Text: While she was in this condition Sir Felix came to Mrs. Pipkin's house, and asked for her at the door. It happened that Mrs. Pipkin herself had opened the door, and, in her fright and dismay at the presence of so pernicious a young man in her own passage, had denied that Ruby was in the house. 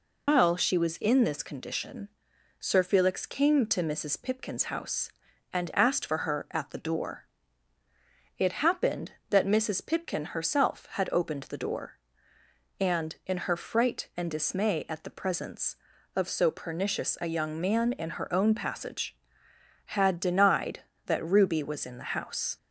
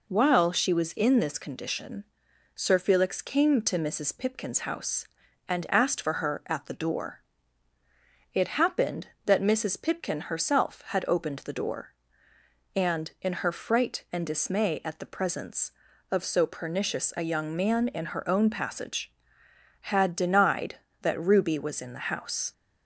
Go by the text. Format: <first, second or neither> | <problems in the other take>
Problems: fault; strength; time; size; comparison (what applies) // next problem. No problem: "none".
second | loses the start of "While"; at 0.2 s; 150 ms // pauses between "condition" and "Sir"; noticeable; at 2.0 s; 0.50 s long; noticeable in the second